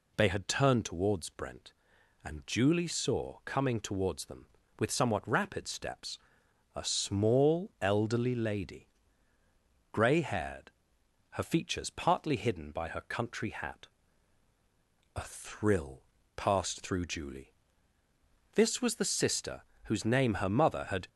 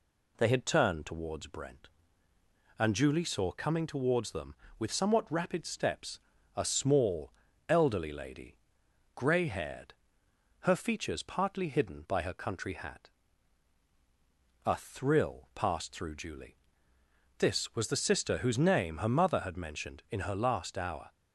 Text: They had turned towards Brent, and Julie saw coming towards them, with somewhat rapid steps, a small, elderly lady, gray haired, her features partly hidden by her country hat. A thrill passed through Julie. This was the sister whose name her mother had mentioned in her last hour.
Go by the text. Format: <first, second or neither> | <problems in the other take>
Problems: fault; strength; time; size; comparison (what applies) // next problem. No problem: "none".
second | pauses between "thrill" and "passed"; slight; at 16.0 s; 0.32 s long // pauses between "sister" and "whose"; slight; at 19.6 s; 0.22 s long // stops before "mentioned in her last hour"; at 21.0 s